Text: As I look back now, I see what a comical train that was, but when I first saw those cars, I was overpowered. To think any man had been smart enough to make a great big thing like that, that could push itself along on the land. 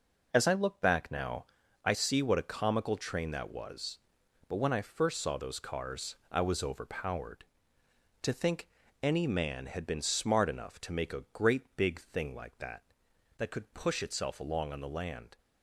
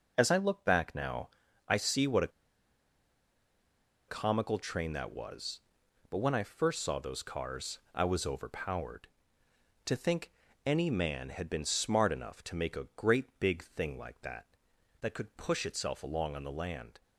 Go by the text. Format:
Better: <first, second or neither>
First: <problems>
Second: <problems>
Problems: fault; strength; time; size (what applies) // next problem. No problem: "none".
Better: first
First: pauses between "think" and "any"; slight; at 8.6 s; 0.34 s long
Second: pauses between "a" and "comical"; strong; at 2.2 s; 1.7 s long // pauses between "think" and "any"; slight; at 10.3 s; 0.34 s long